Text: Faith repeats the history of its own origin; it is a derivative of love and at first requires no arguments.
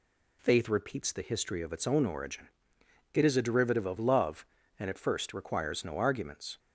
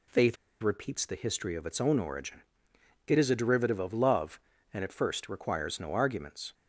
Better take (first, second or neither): first